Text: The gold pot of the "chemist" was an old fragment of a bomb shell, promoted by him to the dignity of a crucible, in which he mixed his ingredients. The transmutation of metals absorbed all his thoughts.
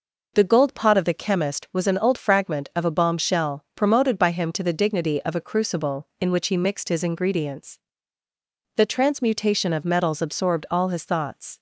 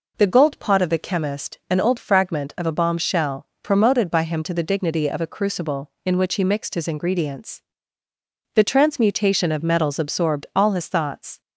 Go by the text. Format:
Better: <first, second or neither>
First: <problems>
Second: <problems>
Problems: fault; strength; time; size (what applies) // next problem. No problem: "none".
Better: first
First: none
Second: skips "was"; at 1.6 s